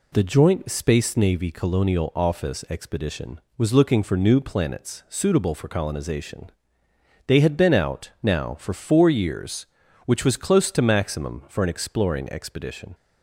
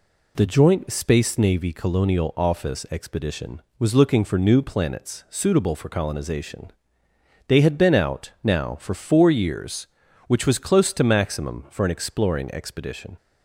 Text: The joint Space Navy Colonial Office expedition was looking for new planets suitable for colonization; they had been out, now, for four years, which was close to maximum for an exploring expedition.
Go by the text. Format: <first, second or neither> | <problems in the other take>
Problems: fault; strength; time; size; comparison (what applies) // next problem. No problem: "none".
neither | none